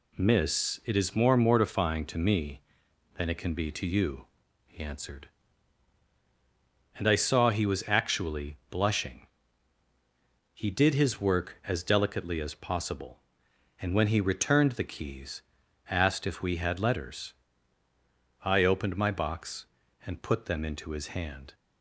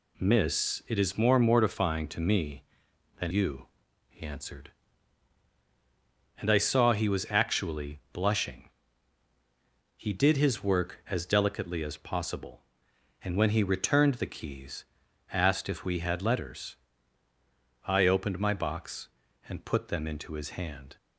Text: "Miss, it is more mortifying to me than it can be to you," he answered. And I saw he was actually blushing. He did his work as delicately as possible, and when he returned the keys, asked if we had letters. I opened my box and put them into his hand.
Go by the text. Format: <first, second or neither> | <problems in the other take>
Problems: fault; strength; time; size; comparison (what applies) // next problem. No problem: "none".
first | skips "it can be to"; at 3.3 s